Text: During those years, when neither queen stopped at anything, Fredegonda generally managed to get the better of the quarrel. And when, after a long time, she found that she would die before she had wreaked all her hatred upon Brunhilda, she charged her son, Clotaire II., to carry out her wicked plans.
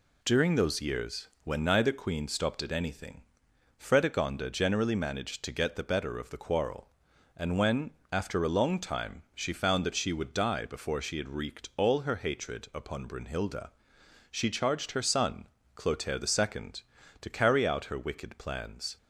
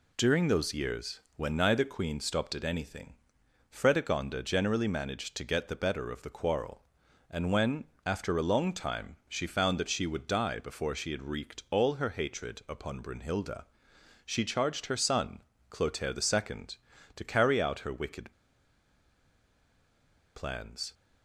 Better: first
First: none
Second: pauses between "wicked" and "plans"; strong; at 18.3 s; 2.0 s long

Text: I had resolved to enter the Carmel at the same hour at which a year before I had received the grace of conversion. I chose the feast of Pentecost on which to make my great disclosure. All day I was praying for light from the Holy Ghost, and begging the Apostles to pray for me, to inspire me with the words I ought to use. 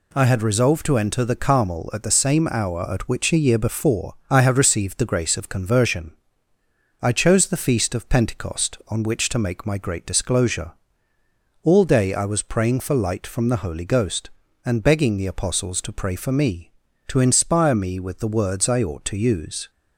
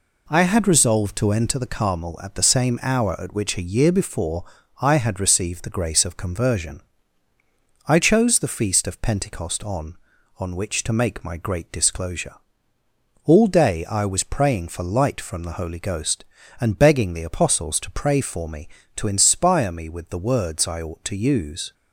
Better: first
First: pauses between "before" and "I"; slight; at 4.1 s; 0.16 s long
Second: pauses between "before" and "I"; at 4.4 s; 0.38 s long // says "on" twice; at 10.3 s

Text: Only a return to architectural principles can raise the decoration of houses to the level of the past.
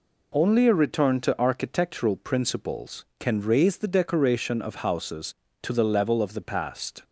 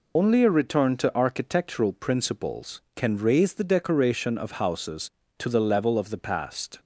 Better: first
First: none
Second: loses the start of "Only"; at 0.1 s; 65 ms

